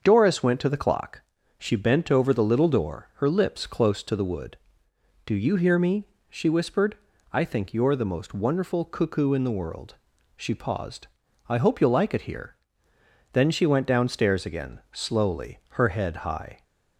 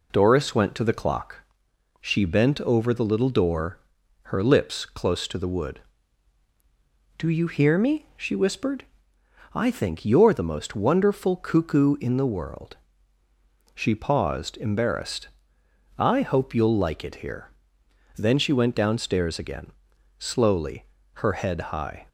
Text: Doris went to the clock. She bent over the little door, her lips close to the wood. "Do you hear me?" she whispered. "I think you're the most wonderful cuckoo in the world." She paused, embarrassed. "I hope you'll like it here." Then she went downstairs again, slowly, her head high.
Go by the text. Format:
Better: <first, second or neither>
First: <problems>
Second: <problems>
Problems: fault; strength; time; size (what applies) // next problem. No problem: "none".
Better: second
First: starts louder than the rest; until 1.0 s; 6.5 dB // skips "embarrassed"; at 11.2 s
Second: none